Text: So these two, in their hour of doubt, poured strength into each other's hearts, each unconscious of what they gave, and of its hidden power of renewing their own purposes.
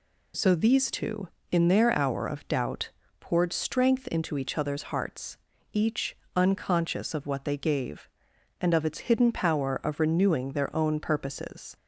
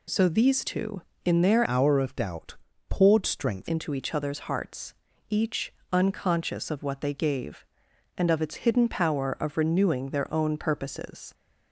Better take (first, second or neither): first